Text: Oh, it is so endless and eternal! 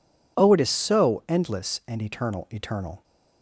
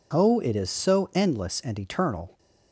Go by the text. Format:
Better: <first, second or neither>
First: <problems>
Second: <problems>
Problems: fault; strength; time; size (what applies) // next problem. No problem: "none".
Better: second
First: says "eternal" twice; at 2.5 s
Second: none